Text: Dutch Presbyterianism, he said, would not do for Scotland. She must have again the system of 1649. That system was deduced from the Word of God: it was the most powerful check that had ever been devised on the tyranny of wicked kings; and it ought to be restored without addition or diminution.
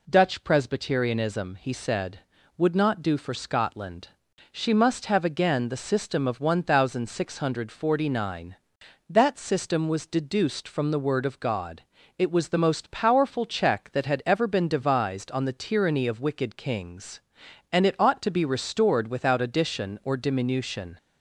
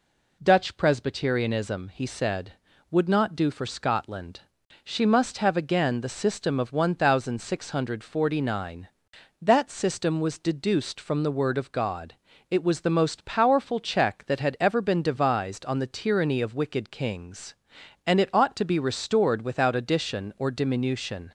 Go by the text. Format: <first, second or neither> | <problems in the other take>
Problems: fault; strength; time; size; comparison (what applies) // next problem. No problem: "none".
neither | none